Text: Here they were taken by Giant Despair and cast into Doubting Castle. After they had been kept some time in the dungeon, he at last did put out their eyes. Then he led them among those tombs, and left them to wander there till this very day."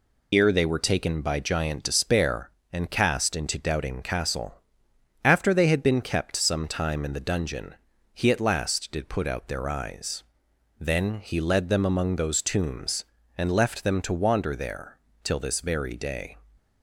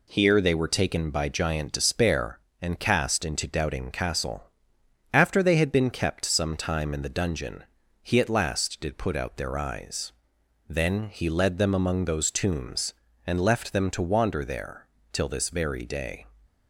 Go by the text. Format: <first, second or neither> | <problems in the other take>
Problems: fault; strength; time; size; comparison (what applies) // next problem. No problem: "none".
second | loses the start of "Here"; at 0.3 s; 115 ms // pauses between "there" and "till"; slight; at 14.9 s; 0.26 s long; slight in the second